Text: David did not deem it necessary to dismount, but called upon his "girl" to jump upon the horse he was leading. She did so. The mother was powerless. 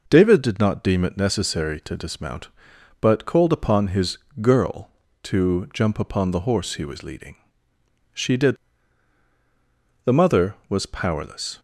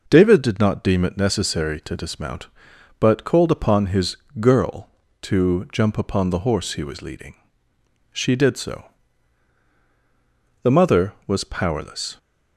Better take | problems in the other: second | pauses between "his" and "girl"; slight; at 4.1 s; 0.22 s long; slight in the second // skips "so"; at 9.3 s

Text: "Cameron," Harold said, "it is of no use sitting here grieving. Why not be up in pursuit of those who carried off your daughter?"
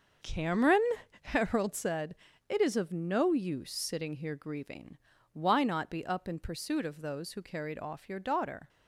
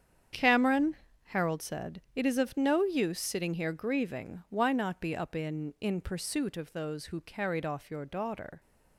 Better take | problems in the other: first | starts louder than the rest; strong; until 1.6 s; 8.5 dB; also in the first // says "in" twice; at 5.7 s

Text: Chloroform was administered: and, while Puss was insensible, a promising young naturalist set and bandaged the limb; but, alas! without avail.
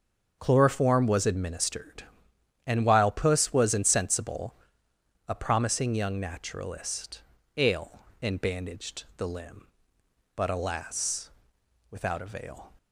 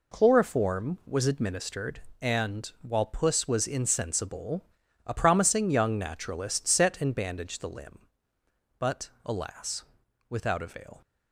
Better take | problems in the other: second | starts louder than the rest; until 1.4 s; 7 dB // says "ale" for "set"; at 7.5 s

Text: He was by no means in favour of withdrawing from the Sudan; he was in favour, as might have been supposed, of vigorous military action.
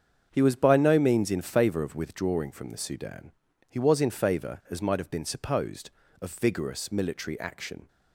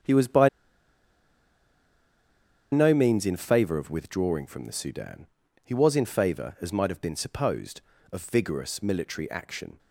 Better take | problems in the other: first | starts louder than the rest; strong; until 3.2 s; 7.5 dB; strong in the first // pauses between "by" and "no"; strong; at 0.4 s; 2.2 s long

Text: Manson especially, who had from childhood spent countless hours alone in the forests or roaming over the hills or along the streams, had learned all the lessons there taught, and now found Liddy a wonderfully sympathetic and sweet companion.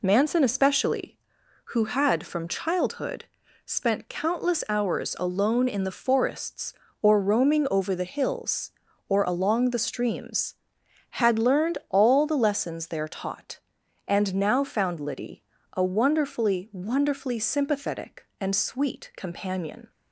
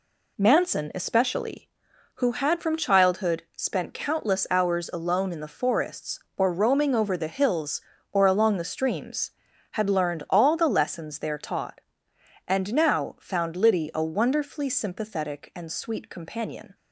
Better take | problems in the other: second | pauses between "childhood" and "spent"; at 3.2 s; 0.42 s long // pauses between "Liddy" and "a"; slight; at 15.4 s; 0.32 s long // says "wonderfully" twice; at 16.7 s

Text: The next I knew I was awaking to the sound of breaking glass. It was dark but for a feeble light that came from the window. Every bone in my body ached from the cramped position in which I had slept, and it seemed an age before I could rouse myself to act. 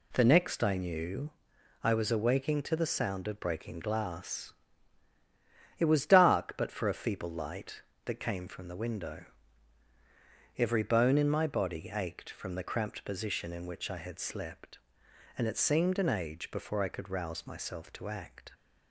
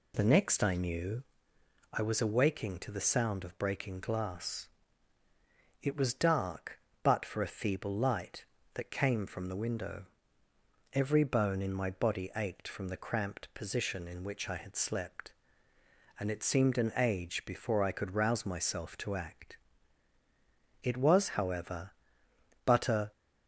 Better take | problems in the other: first | pauses between "knew" and "I"; noticeable; at 1.2 s; 0.68 s long; noticeable in the first // goes on to say "It was however but a"; strong; from 20.8 s on; 2.3 s long

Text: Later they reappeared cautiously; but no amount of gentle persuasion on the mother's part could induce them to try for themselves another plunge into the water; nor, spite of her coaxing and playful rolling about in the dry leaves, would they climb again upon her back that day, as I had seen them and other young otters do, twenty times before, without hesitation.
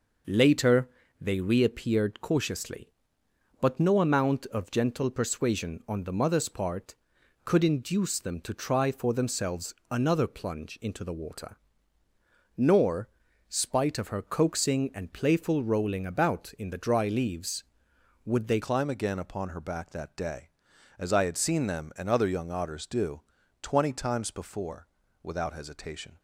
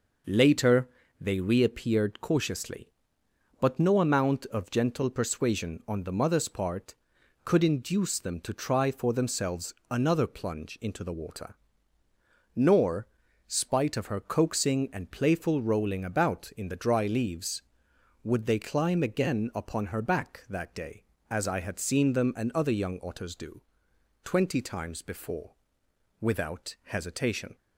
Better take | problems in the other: second | pauses between "Later" and "they"; slight; at 0.8 s; 0.32 s long; slight in the second // pauses between "themselves" and "another"; slight; at 9.7 s; 0.16 s long; slight in the second // changes voice at "climb"; from 18.6 s on; 7.5 s long

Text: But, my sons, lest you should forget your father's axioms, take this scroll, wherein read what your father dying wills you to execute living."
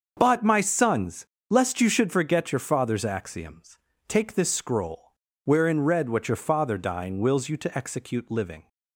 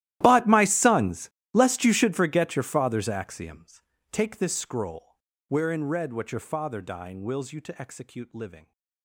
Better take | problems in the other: first | gets quieter; strong; throughout; 22 dB // starts louder than the rest; strong; until 1.2 s; 14 dB; also in the first

